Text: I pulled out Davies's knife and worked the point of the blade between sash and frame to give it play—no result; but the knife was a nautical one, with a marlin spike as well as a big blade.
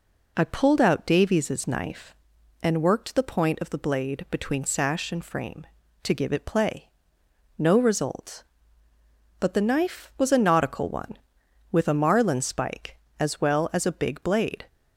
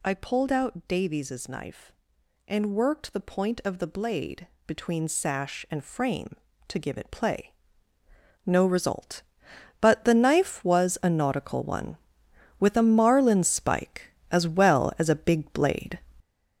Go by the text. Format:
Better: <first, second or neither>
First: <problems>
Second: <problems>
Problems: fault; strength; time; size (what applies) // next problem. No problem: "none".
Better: first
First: none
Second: gets louder; strong; throughout; 7.5 dB // pauses between "blade" and "between"; slight; at 4.4 s; 0.18 s long